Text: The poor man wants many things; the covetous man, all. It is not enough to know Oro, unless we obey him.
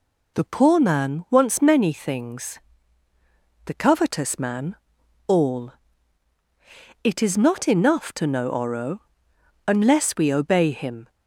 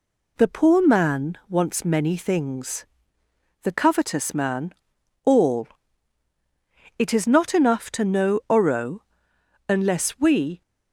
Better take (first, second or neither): first